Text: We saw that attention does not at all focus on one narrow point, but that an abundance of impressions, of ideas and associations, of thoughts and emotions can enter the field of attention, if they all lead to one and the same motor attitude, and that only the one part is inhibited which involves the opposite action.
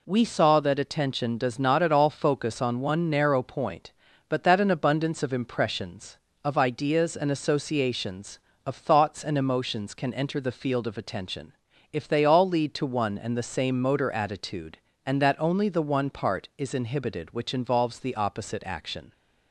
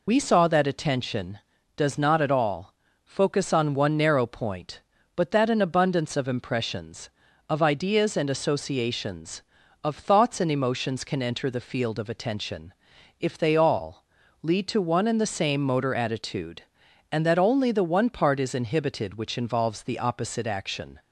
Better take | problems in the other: first | loses the start of "We"; at 0.0 s; 65 ms // pauses between "all" and "focus"; slight; at 2.7 s; 0.32 s long // pauses between "all" and "lead"; slight; at 14.0 s; 0.36 s long

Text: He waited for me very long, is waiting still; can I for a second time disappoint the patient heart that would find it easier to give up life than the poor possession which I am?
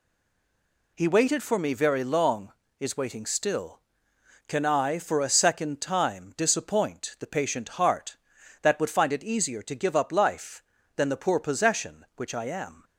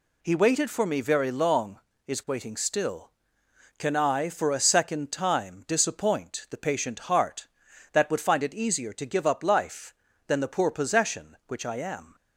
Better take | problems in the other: second | stays silent before the first word; slight; until 0.9 s; 0.9 s long

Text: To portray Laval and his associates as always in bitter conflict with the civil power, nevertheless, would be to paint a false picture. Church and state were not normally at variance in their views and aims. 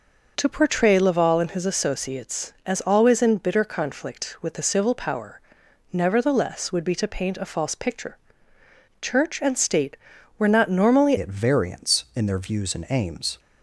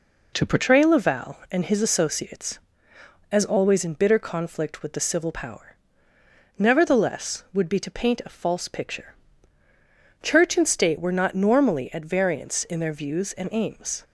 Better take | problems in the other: second | changes voice at "at"; from 11.1 s on; 2.2 s long

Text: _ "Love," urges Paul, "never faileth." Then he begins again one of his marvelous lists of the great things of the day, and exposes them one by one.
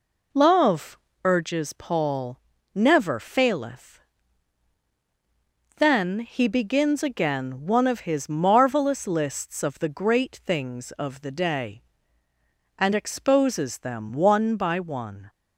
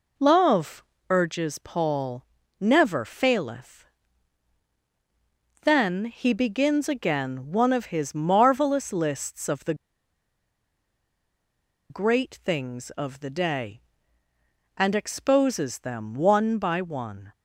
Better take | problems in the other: first | pauses between "the" and "great"; strong; at 9.7 s; 2.1 s long

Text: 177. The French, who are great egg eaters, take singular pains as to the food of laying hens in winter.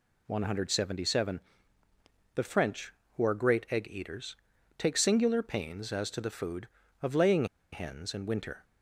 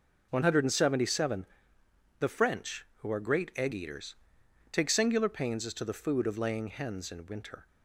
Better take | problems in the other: second | pauses between "laying" and "hens"; slight; at 7.4 s; 0.27 s long

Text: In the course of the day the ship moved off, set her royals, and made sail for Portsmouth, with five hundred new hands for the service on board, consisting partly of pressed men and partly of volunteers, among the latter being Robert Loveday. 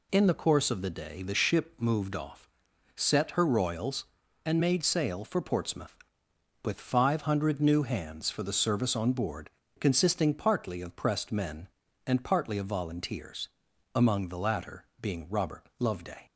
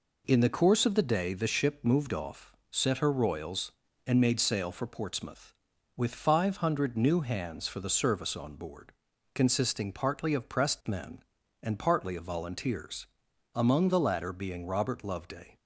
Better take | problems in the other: neither | none

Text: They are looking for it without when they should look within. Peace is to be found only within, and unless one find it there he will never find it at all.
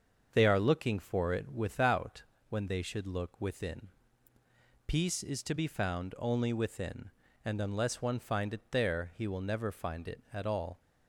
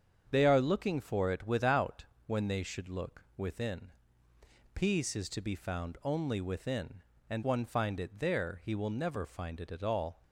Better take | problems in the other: first | starts louder than the rest; strong; until 1.3 s; 7.5 dB; also in the first // pauses between "without" and "when"; slight; at 2.0 s; 0.22 s long; slight in the first // skips "unless"; at 7.4 s

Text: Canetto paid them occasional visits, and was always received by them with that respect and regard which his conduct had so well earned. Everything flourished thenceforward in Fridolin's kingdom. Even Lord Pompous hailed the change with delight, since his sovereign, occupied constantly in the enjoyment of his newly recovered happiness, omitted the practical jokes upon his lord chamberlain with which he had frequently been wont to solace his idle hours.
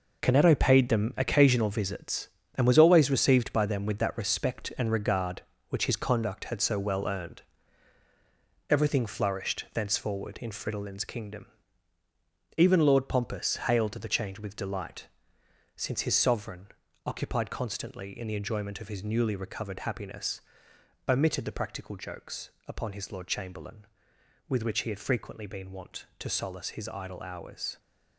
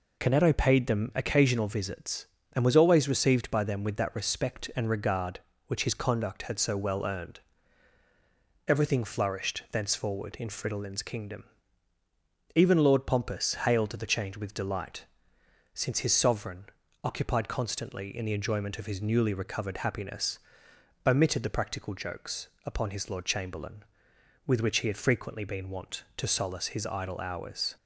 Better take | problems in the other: second | gets quieter; strong; throughout; 9.5 dB // pauses between "jokes" and "upon"; slight; at 22.5 s; 0.16 s long; slight in the second

